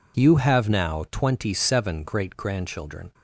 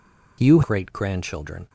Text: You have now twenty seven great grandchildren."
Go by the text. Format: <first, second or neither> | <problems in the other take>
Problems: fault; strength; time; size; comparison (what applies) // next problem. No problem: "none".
first | skips "have now twenty seven"; at 0.6 s